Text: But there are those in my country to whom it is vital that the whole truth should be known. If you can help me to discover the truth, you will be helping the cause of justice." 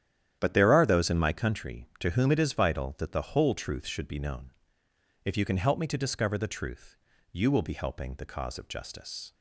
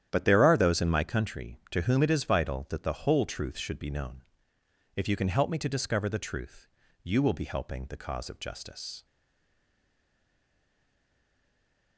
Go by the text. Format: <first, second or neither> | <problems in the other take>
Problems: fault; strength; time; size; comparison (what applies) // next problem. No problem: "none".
first | starts louder than the rest; strong; until 1.1 s; 10.5 dB; strong in the first // stays silent after the last word; strong; from 9.0 s on; 2.9 s long